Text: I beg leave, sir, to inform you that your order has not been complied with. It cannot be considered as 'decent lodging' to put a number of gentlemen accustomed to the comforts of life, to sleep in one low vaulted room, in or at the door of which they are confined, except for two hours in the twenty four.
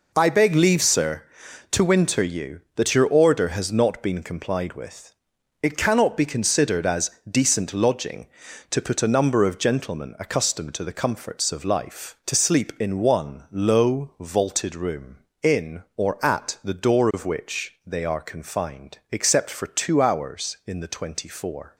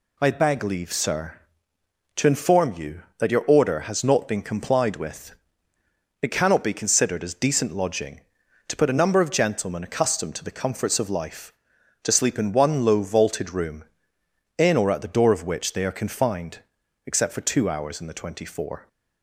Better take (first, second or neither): second